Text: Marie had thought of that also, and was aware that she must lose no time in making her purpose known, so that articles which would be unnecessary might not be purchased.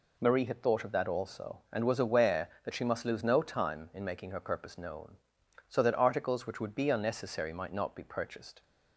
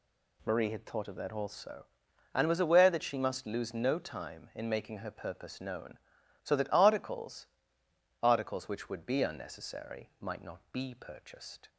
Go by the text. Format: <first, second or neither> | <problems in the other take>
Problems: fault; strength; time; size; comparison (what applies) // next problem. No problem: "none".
first | says "articles" twice; at 8.2 s